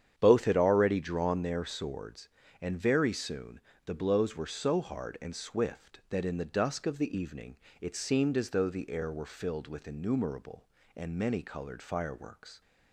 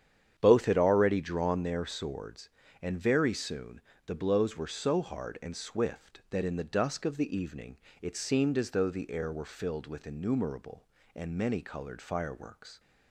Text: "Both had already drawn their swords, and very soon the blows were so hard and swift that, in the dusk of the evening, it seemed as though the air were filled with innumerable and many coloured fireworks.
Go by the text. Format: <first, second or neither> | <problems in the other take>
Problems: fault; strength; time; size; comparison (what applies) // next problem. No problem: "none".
neither | starts louder than the rest; strong; the same in both // pauses between "soon" and "the"; slight; the same in both